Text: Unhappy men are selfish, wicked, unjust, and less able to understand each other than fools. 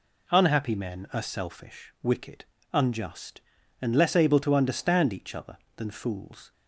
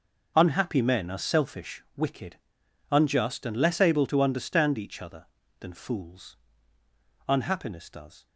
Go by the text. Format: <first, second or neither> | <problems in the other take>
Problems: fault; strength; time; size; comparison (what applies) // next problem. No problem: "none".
first | goes on to say "Unhappiness does"; noticeable; from 7.2 s on; 1.0 s long